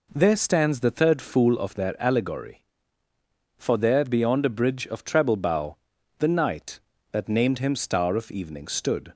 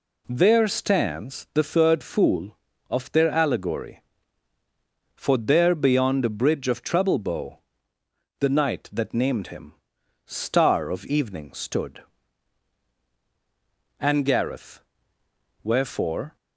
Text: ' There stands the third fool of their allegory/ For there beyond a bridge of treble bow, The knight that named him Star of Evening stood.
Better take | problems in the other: first | pauses between "him" and "Star"; noticeable; at 9.7 s; 0.52 s long // goes on to say "And Gareth Wherefore"; strong; from 13.9 s on; 2.3 s long

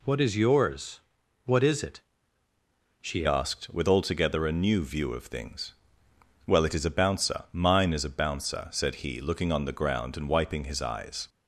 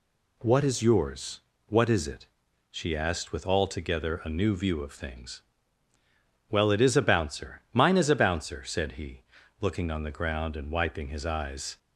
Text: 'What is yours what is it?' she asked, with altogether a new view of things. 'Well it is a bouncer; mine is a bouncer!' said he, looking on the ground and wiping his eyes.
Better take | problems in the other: second | pauses between "yours" and "what"; at 0.9 s; 0.44 s long; slight in the second // changes voice at "asked"; from 3.2 s on; 8.0 s long

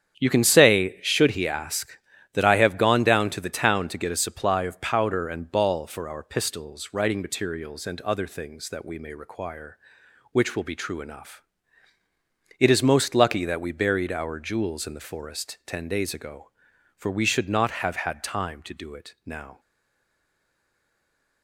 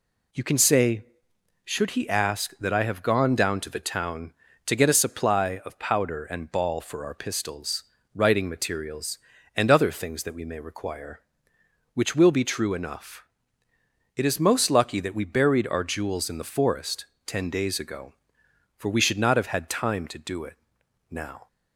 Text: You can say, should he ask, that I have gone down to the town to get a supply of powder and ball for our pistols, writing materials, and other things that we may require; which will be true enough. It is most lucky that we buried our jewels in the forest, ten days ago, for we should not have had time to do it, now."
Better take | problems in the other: second | starts louder than the rest; strong; until 1.2 s; 8.5 dB // stays silent after the last word; noticeable; from 19.5 s on; 1.9 s long

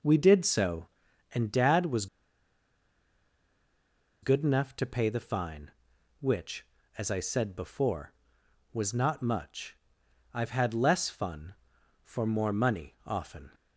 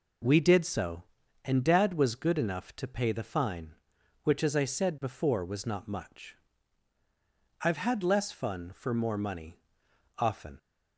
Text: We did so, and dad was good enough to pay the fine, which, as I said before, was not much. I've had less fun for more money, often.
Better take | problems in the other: second | pauses between "was" and "good"; strong; at 2.0 s; 2.1 s long

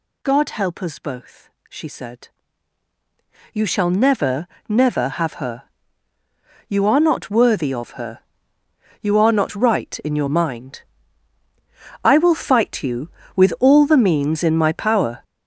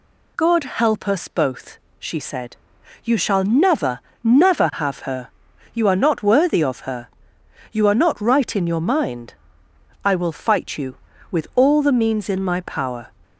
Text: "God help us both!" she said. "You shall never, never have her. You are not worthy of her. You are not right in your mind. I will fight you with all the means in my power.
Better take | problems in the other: second | gets louder; strong; throughout; 9 dB

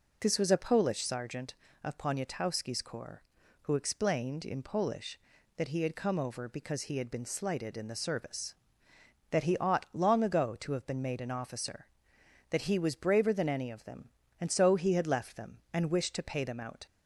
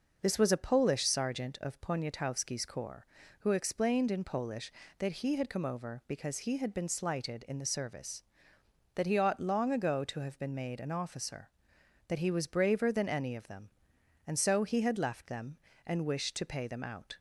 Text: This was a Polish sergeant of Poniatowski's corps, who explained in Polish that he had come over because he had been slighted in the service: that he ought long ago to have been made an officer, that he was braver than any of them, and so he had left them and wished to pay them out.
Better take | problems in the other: neither | none

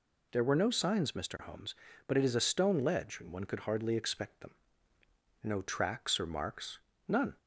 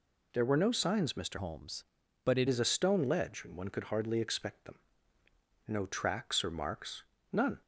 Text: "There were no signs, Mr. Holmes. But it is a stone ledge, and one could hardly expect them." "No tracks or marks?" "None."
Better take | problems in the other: first | changes voice from "Holmes" to "it"; from 1.3 to 2.4 s; 1.1 s long

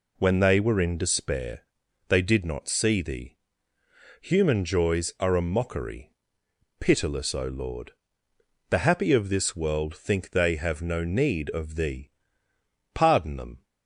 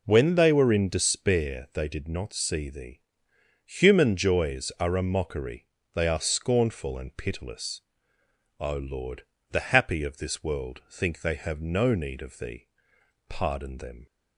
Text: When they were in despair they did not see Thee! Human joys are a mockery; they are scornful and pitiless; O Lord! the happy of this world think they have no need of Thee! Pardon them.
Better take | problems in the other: second | pauses between "despair" and "they"; noticeable; at 1.6 s; 0.46 s long // skips "they are scornful and"; at 6.4 s

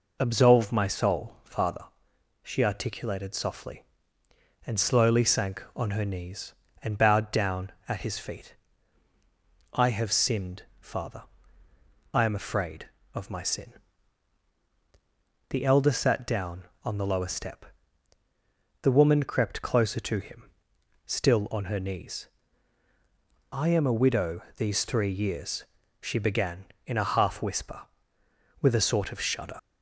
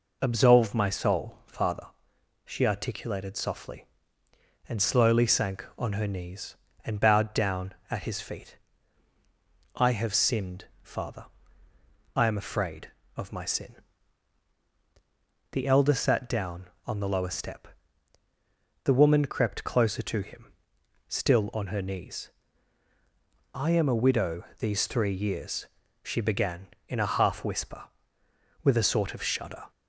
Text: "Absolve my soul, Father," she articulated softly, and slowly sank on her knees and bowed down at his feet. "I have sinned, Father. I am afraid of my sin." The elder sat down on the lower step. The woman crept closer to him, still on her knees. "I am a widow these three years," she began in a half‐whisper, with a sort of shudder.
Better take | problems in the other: second | leaves "shudder" unfinished; at 29.5 s; 85 ms

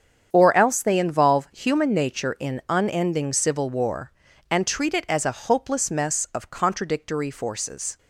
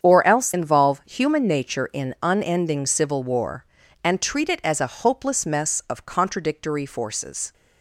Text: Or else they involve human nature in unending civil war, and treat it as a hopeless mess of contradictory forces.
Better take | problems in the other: first | starts louder than the rest; strong; until 1.0 s; 8 dB; strong in the first // skips "they"; at 0.5 s

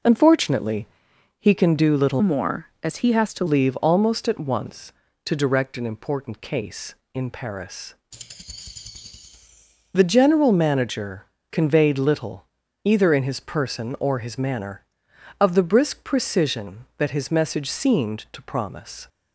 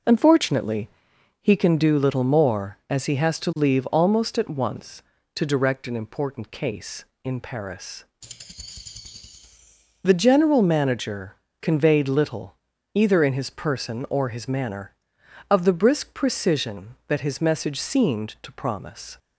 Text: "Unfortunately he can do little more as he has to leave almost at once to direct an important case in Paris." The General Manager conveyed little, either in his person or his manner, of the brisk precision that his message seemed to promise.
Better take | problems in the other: second | pauses between "Unfortunately" and "he"; noticeable; at 0.8 s; 0.52 s long; noticeable in the second // changes voice from "more" to "to"; from 2.2 to 3.4 s; 1.2 s long // pauses between "Manager" and "conveyed"; slight; at 11.2 s; 0.26 s long; slight in the second

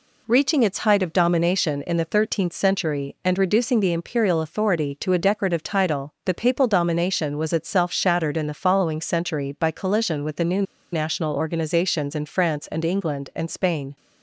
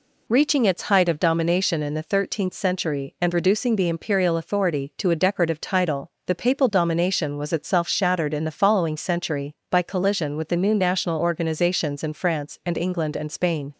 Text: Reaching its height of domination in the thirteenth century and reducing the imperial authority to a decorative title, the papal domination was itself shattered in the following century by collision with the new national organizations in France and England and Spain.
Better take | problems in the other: second | pauses between "new" and "national"; slight; at 10.6 s; 0.29 s long

